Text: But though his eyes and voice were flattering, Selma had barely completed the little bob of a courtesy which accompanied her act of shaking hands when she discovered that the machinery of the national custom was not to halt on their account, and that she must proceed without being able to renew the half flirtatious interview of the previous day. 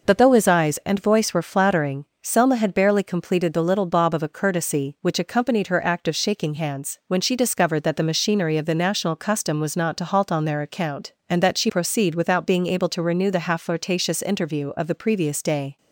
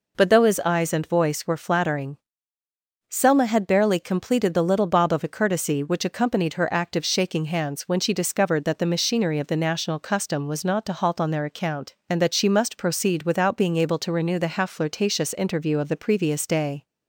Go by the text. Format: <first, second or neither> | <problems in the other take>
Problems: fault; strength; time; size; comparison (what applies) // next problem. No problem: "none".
second | skips "must"; at 11.6 s